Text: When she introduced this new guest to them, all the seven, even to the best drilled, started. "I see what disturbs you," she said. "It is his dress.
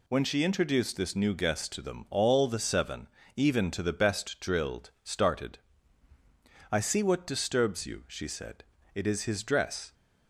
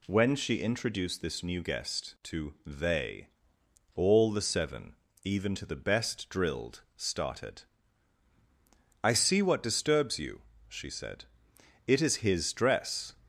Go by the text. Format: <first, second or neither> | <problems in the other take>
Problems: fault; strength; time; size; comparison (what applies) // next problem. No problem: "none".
first | says "they" for "them"; at 2.6 s